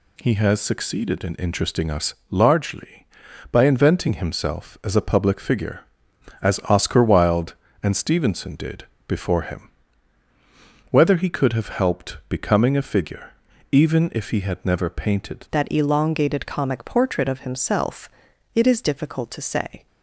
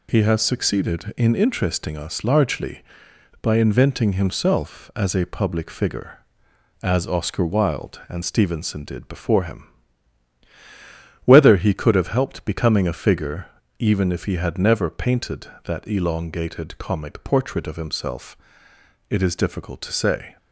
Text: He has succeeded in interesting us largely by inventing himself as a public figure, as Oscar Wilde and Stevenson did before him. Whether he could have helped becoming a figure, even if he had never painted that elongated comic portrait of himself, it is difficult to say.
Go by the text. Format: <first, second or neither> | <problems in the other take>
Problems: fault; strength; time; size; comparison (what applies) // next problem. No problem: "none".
second | pauses between "us" and "largely"; slight; at 2.1 s; 0.16 s long // pauses between "did" and "before"; slight; at 8.8 s; 0.20 s long // changes voice at "that"; from 15.5 s on; 4.3 s long